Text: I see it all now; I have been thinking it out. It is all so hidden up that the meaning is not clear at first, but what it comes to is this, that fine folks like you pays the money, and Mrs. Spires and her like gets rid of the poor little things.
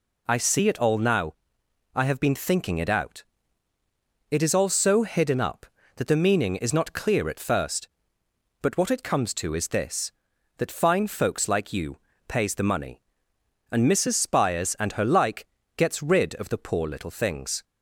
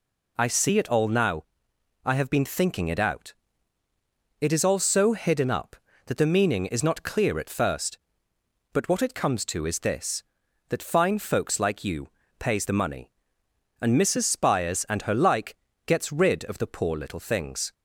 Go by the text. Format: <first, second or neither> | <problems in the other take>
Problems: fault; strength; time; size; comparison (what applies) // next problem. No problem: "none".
neither | pauses between "you" and "pays"; slight; the same in both // pauses between "like" and "gets"; slight; the same in both